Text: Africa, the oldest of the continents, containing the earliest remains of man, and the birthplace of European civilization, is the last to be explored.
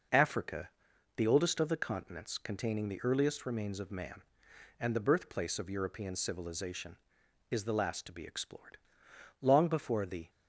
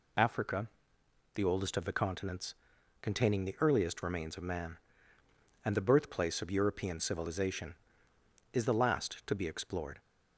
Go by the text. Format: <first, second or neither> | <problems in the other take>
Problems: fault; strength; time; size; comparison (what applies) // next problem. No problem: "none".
second | goes on to say "Long before the"; noticeable; from 9.4 s on; 0.88 s long